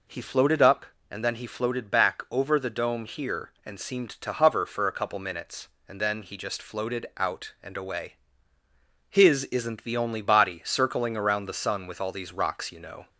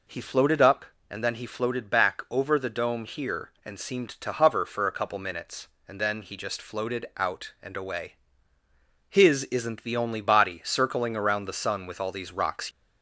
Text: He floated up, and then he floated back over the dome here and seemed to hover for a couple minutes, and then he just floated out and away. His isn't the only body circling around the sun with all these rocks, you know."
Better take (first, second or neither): first